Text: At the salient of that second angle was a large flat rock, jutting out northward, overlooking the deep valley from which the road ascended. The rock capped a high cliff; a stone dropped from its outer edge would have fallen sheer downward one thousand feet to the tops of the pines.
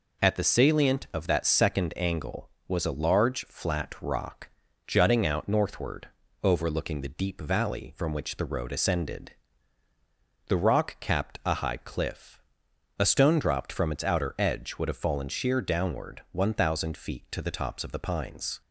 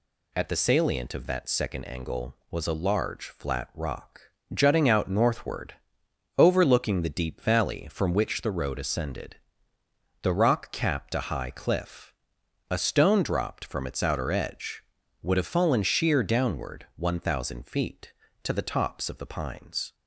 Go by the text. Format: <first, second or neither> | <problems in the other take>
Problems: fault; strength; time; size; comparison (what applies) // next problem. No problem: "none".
neither | none